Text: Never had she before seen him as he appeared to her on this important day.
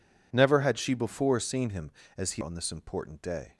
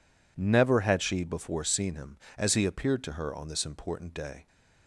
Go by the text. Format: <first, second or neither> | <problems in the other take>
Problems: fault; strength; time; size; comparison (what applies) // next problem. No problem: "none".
second | skips "appeared to her"; at 2.4 s